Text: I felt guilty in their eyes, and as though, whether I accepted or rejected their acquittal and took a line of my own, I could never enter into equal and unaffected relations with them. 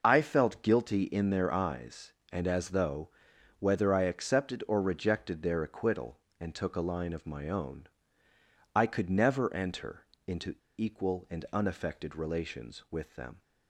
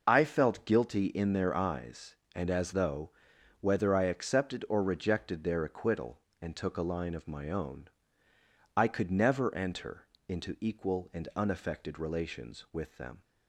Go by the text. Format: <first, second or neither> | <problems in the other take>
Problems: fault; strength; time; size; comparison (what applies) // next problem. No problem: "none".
second | pauses between "enter" and "into"; slight; at 10.0 s; 0.22 s long; slight in the second // pauses between "into" and "equal"; slight; at 10.5 s; 0.24 s long